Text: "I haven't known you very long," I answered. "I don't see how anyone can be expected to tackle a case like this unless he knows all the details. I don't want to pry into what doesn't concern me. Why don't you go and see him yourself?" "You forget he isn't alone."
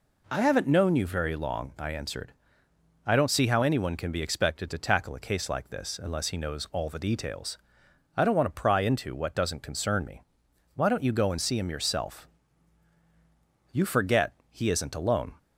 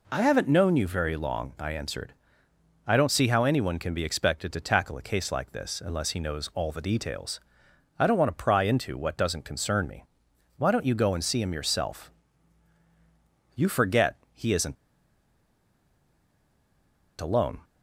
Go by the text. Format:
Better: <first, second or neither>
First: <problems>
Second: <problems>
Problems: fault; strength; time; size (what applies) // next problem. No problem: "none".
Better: first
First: pauses between "forget" and "he"; slight; at 14.3 s; 0.16 s long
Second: pauses between "forget" and "he"; slight; at 14.1 s; 0.16 s long // pauses between "isn't" and "alone"; strong; at 14.7 s; 2.4 s long